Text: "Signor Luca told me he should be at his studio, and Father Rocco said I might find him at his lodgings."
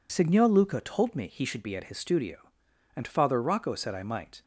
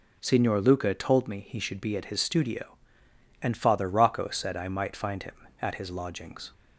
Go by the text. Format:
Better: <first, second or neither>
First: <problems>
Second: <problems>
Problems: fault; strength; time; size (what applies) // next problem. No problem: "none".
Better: second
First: stops before "find him at his lodgings"; at 4.4 s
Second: none